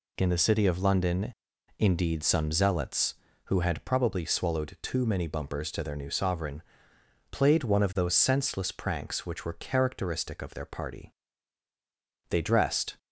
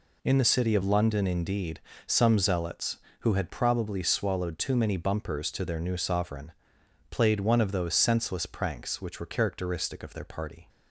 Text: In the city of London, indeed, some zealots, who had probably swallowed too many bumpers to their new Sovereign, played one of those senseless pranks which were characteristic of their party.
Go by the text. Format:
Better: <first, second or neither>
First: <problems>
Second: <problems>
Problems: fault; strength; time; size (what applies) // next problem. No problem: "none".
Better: second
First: goes on to say "They dressed"; noticeable; from 12.2 s on; 0.68 s long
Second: none